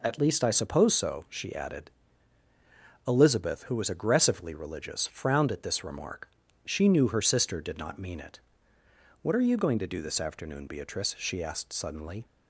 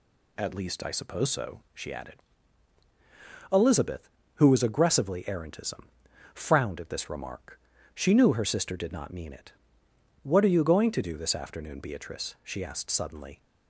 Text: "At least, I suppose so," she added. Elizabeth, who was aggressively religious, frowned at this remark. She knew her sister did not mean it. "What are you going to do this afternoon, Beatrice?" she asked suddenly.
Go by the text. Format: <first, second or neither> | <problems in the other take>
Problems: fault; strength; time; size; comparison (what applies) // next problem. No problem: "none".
first | says "errantism" for "religious"; at 5.2 s